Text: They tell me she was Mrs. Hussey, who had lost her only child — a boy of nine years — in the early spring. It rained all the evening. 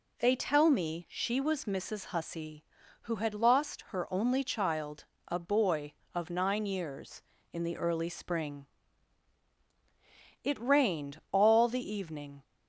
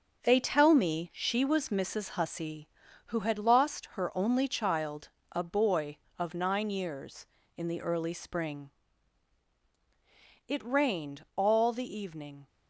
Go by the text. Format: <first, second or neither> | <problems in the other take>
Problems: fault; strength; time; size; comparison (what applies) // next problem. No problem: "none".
first | gets quieter; throughout; 6.5 dB